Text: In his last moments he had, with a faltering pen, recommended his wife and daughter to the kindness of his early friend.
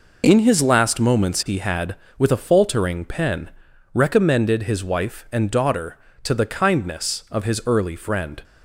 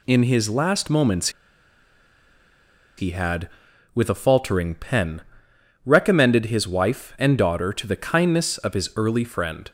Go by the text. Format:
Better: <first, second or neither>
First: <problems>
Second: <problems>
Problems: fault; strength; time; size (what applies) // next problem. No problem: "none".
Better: first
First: none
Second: pauses between "moments" and "he"; strong; at 1.2 s; 1.6 s long